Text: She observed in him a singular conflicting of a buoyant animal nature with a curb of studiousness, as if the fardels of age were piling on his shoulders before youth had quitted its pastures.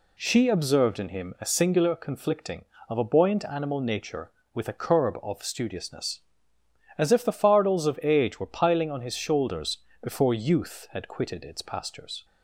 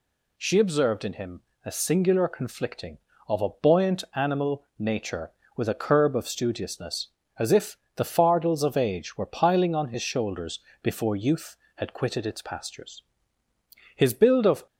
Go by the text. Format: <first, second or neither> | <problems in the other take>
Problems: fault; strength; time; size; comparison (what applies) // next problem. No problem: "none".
first | pauses between "him" and "a"; slight; at 1.3 s; 0.24 s long // pauses between "if" and "the"; slight; at 7.7 s; 0.20 s long // pauses between "shoulders" and "before"; slight; at 10.5 s; 0.22 s long; slight in the first // goes on to say "His build of"; noticeable; from 13.9 s on; 0.70 s long